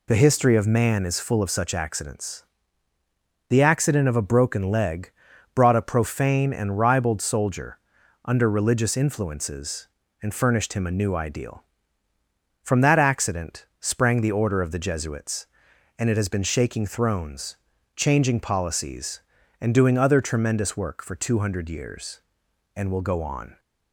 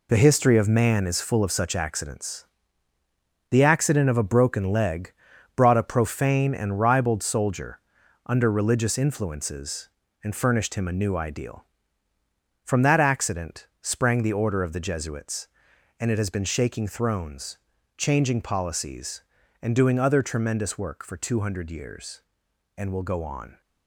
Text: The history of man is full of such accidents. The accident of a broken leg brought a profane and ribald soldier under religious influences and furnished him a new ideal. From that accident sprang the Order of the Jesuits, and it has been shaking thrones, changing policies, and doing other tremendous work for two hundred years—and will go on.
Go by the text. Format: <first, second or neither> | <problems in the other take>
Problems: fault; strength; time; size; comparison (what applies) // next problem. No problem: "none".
first | gets quieter; strong; throughout; 9 dB // pauses between "leg" and "brought"; at 5.1 s; 0.42 s long; also in the first // pauses between "soldier" and "under"; noticeable; at 7.7 s; 0.48 s long; noticeable in the first